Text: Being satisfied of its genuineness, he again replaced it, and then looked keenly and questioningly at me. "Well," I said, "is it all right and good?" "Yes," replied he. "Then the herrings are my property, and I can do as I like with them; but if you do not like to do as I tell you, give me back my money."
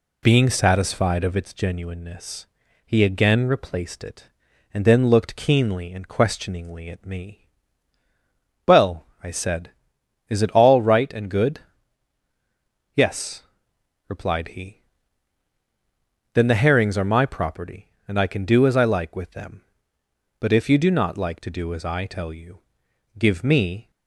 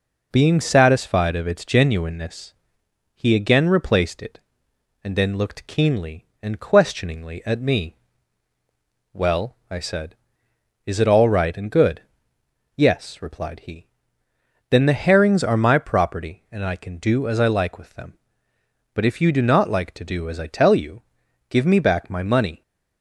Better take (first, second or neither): second